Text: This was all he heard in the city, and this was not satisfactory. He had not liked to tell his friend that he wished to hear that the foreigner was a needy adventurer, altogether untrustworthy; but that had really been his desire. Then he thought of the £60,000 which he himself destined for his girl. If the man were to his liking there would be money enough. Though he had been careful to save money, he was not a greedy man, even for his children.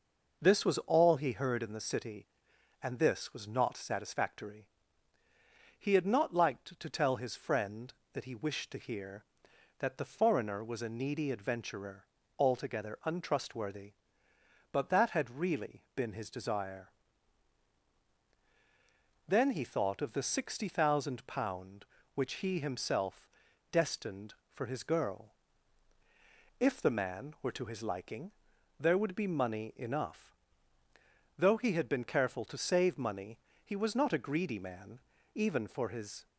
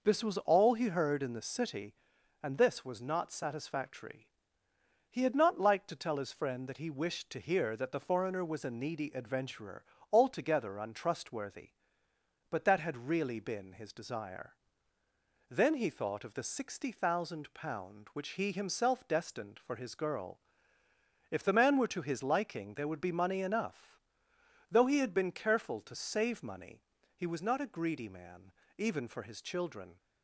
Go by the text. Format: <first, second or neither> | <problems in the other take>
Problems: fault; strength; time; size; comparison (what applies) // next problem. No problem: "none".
second | pauses between "himself" and "destined"; at 23.2 s; 0.44 s long // pauses between "liking" and "there"; noticeable; at 28.2 s; 0.50 s long // stops before "children"; at 36.2 s